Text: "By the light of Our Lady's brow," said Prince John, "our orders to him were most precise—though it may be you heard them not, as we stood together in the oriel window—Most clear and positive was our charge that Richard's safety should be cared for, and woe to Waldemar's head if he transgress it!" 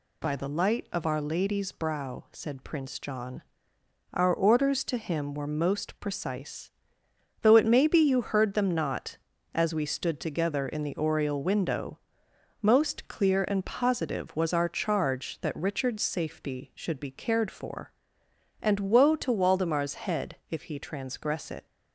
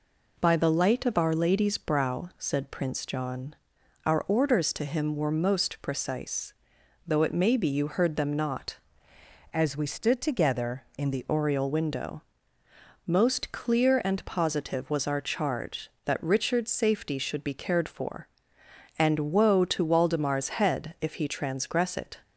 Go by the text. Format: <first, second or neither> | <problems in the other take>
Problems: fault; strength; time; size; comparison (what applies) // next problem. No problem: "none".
first | changes voice from "as" to "the"; from 9.5 to 11.2 s; 1.7 s long